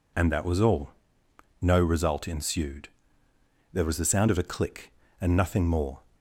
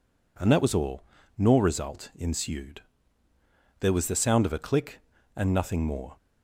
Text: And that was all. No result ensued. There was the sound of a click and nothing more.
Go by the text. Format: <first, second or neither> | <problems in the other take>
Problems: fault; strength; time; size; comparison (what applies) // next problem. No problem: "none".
first | says "Nor" for "No"; at 1.3 s